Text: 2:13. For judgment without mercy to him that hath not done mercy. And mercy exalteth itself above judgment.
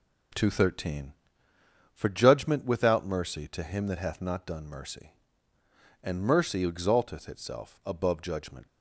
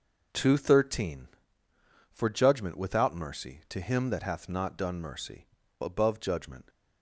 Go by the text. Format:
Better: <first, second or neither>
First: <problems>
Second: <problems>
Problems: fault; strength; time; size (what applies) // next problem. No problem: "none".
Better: first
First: none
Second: skips "And mercy exalteth itself"; at 5.6 s